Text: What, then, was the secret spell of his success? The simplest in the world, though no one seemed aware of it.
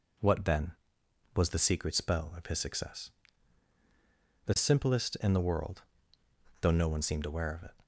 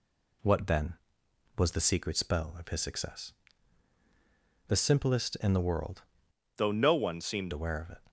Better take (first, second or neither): first